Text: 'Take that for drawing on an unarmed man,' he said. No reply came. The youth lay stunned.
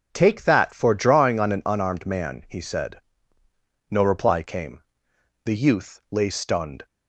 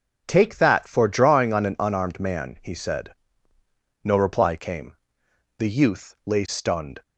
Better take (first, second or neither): neither